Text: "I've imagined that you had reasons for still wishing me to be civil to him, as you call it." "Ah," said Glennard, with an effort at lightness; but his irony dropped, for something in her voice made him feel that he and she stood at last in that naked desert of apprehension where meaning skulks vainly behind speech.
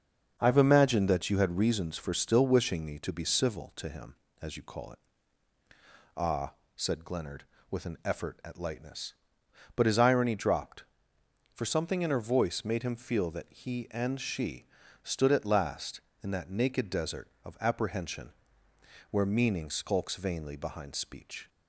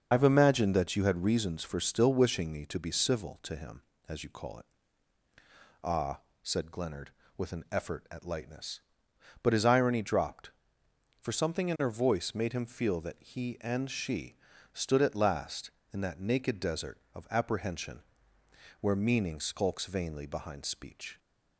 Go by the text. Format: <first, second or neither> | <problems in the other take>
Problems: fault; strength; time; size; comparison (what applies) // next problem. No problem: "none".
first | loses the start of "I've"; at 0.1 s; 60 ms // starts louder than the rest; until 1.1 s; 6.5 dB; also in the first // pauses between "she" and "stood"; slight; at 14.3 s; 0.36 s long; slight in the first // pauses between "apprehension" and "where"; noticeable; at 18.0 s; 0.78 s long; noticeable in the first